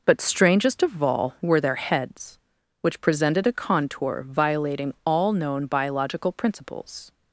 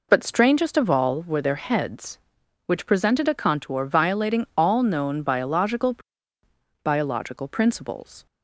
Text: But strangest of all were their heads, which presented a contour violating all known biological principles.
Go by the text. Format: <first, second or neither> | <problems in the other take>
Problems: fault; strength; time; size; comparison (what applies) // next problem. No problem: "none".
first | says "biological" twice; at 6.8 s